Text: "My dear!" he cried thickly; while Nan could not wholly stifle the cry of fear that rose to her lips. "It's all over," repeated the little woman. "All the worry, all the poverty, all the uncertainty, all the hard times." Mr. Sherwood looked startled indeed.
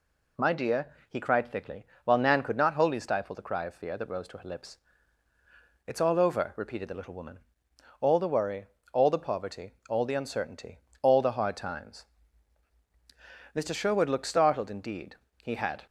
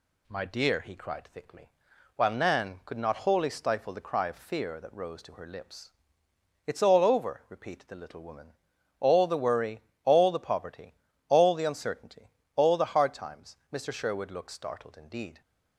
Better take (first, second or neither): second